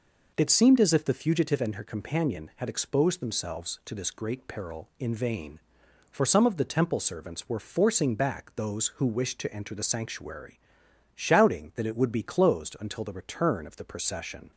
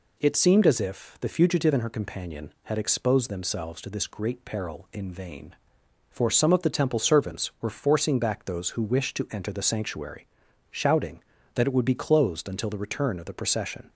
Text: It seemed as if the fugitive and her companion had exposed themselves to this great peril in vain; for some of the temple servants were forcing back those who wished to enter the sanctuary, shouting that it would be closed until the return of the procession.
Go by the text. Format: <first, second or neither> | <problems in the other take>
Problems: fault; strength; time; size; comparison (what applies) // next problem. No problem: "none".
neither | none